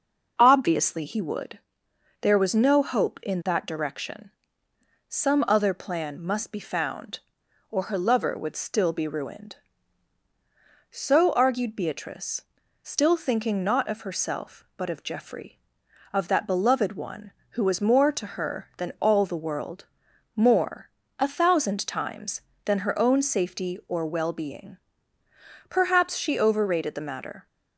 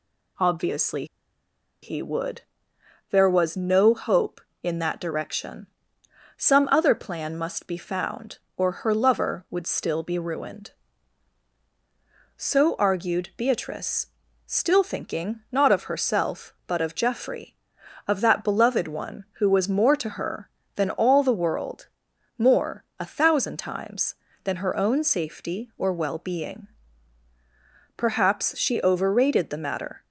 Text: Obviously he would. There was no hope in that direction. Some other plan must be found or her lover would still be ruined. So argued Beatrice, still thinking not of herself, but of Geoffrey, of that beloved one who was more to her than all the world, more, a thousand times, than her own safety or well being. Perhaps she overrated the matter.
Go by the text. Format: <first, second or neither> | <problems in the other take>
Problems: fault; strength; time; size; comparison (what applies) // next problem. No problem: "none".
first | pauses between "Obviously" and "he"; noticeable; at 1.0 s; 0.78 s long